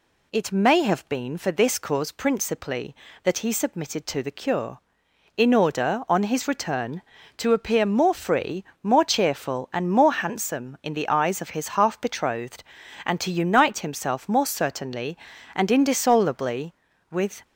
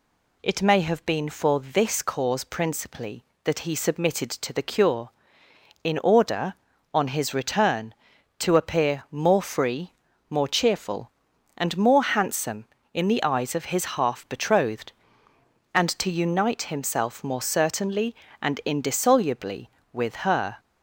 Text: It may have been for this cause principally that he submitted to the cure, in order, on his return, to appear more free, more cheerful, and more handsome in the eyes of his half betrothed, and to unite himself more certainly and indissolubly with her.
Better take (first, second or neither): second